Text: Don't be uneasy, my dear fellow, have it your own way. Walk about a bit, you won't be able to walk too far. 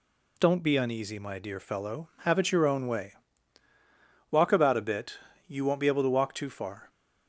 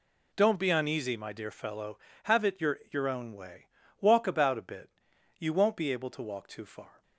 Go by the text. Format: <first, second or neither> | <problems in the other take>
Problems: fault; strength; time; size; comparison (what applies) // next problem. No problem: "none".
first | says "your" twice; at 2.8 s